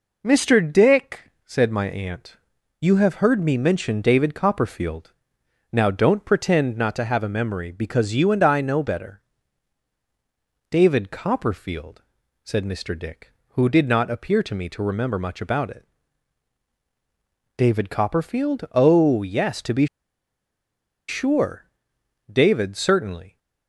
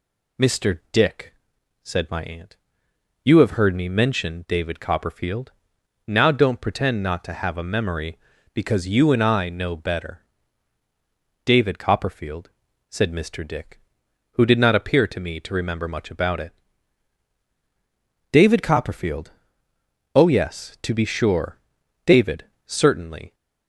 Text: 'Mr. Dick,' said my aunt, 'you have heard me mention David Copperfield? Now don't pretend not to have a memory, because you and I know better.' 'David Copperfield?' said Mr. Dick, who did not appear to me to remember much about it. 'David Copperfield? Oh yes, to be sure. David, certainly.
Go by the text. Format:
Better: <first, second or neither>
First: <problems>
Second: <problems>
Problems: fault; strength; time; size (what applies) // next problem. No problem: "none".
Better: second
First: pauses between "be" and "sure"; at 19.8 s; 1.2 s long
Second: none